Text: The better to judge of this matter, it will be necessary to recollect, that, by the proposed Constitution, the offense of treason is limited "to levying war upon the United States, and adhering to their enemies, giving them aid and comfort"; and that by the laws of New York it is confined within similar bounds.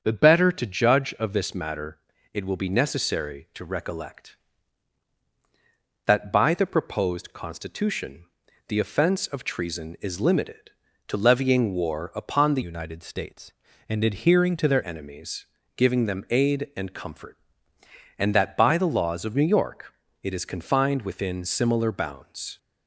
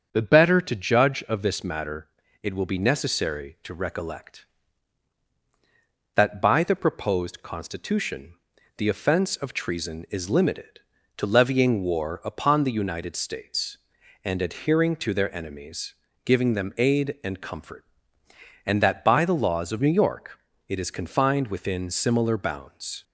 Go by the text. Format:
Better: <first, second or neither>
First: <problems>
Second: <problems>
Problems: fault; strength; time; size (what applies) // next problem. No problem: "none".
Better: second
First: starts louder than the rest; strong; until 1.0 s; 7 dB // changes voice from "United" to "their"; from 12.6 to 14.8 s; 2.2 s long // pauses between "York" and "it"; slight; at 19.9 s; 0.30 s long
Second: starts louder than the rest; strong; until 1.1 s; 7 dB // pauses between "York" and "it"; slight; at 20.3 s; 0.30 s long